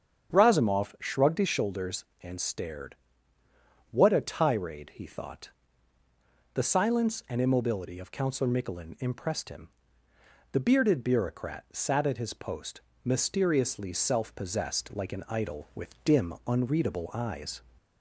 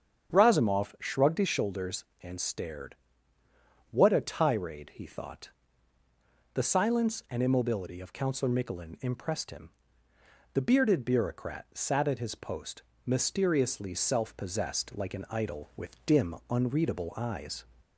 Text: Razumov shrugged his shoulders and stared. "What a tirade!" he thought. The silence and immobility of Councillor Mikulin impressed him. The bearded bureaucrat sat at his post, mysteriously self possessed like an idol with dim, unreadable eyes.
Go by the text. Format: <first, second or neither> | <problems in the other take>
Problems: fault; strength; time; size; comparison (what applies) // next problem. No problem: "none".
neither | starts louder than the rest; strong; the same in both